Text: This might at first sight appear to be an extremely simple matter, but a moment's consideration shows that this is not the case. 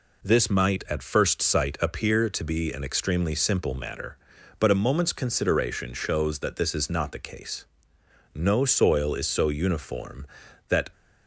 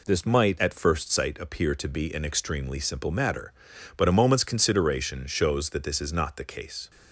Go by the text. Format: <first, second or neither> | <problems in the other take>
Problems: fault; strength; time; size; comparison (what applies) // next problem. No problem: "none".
second | goes on to say "No soil is so uniform that"; strong; from 8.3 s on; 2.5 s long